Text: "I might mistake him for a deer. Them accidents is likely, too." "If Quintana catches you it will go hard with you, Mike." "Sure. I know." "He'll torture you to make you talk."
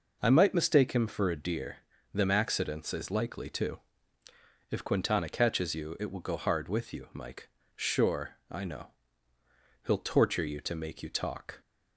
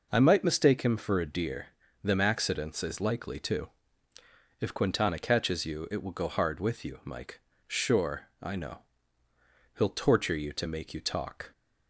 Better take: neither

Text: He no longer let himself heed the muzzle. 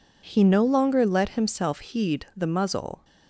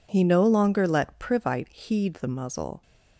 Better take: first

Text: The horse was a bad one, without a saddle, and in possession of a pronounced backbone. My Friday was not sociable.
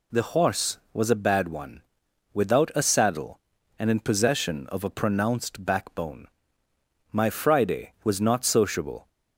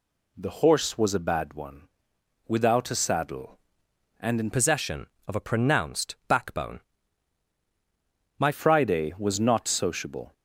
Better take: first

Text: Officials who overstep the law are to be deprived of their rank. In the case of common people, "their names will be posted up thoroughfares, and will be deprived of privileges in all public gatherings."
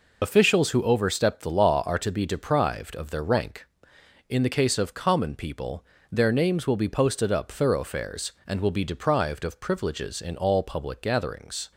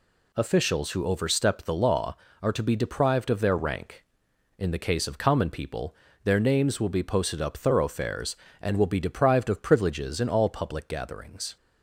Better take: second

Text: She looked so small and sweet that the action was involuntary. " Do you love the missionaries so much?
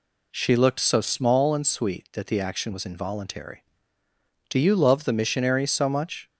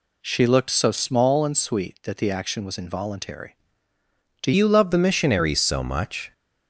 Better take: first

